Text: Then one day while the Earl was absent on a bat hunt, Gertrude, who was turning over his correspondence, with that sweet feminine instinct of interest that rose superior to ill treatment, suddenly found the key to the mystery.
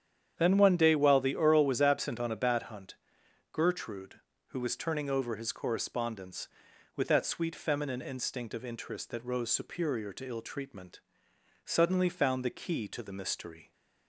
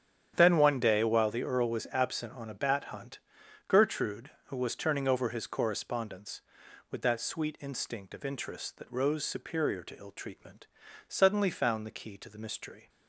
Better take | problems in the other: first | starts louder than the rest; strong; until 1.3 s; 9 dB; strong in the first // skips "feminine"; at 7.5 s

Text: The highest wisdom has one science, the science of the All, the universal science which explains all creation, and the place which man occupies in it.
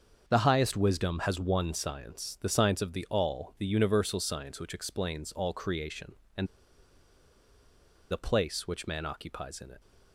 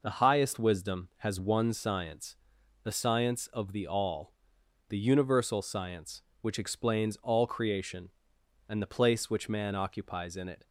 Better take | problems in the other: second | starts louder than the rest; until 1.2 s; 7 dB // pauses between "and" and "the"; strong; at 6.4 s; 1.6 s long

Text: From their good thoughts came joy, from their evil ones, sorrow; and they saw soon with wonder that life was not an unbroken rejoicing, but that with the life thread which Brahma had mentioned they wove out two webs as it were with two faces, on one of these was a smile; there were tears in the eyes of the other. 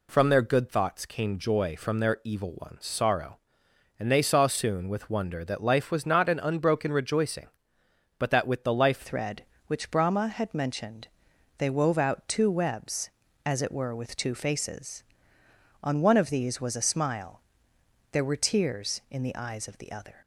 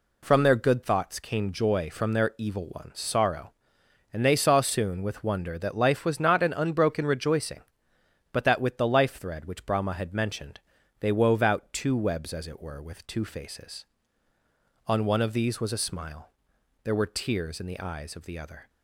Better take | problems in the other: second | changes voice at "thread"; from 9.0 s on; 11.1 s long // pauses between "mentioned" and "they"; noticeable; at 11.0 s; 0.50 s long; also in the second

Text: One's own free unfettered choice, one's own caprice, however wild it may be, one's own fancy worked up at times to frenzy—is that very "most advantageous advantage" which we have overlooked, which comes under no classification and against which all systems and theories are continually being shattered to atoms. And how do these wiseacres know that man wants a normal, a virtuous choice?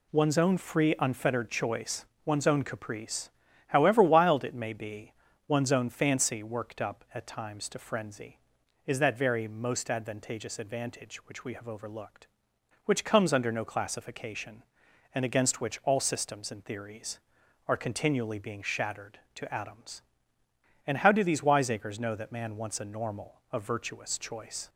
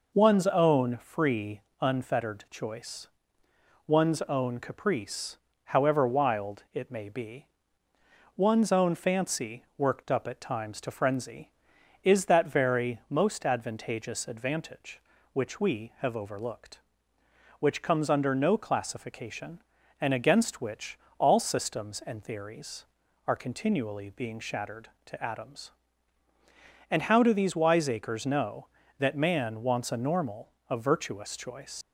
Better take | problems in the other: first | pauses between "free" and "unfettered"; slight; at 1.6 s; 0.20 s long // pauses between "which" and "all"; slight; at 20.9 s; 0.22 s long // leaves "choice" unfinished; at 31.8 s; 120 ms

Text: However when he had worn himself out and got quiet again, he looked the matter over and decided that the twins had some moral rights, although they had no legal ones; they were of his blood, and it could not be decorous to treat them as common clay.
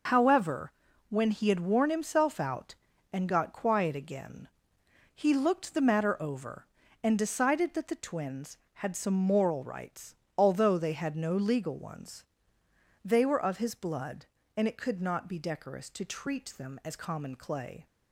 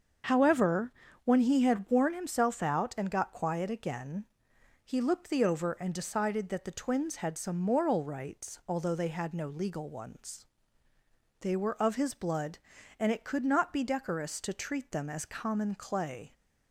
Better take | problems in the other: first | starts louder than the rest; until 1.5 s; 6.5 dB // pauses between "However" and "when"; slight; at 0.9 s; 0.34 s long; also in the first // skips "matter"; at 5.4 s

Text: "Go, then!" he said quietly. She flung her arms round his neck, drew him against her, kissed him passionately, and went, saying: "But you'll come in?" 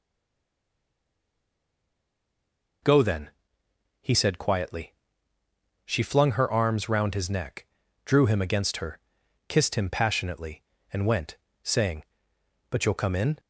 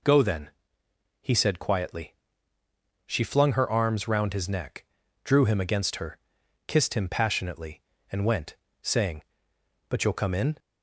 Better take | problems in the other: second | stays silent before the first word; strong; until 2.8 s; 2.8 s long

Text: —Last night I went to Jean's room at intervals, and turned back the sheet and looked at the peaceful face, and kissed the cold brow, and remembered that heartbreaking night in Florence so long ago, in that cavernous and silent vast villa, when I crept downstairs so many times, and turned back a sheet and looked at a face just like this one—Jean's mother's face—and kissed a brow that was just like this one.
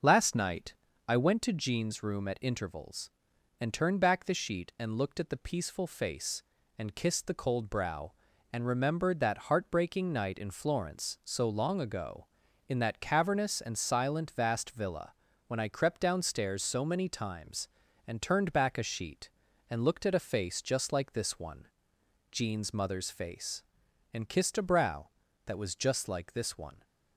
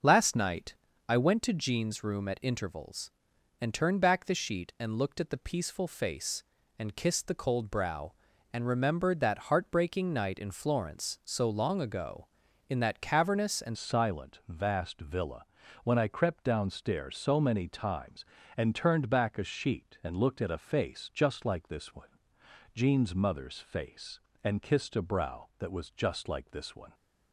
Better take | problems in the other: first | starts louder than the rest; until 1.3 s; 6.5 dB; also in the first // pauses between "night" and "I"; slight; at 0.7 s; 0.34 s long; slight in the first // changes voice at "silent"; from 13.7 s on; 13.2 s long

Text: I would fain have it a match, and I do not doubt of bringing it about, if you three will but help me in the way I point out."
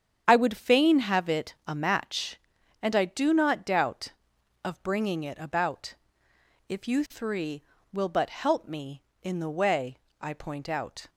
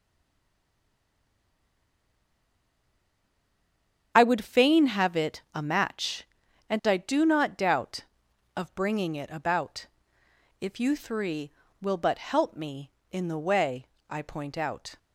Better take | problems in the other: first | stays silent before the first word; strong; until 4.1 s; 4.1 s long // starts louder than the rest; strong; until 5.1 s; 8 dB; strong in the first // pauses between "way" and "I"; slight; at 13.8 s; 0.20 s long; slight in the first

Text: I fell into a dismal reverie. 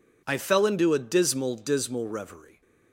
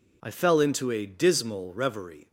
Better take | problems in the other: second | says "dismal" twice; at 1.5 s

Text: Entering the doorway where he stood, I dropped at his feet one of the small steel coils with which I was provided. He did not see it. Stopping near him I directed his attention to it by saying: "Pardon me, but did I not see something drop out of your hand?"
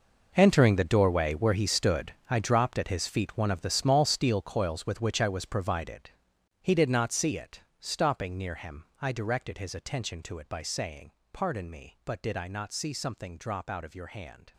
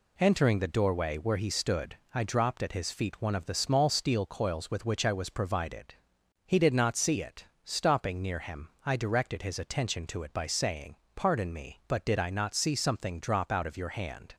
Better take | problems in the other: second | gets quieter; strong; throughout; 14.5 dB // pauses between "him" and "I"; slight; at 8.8 s; 0.16 s long; slight in the second

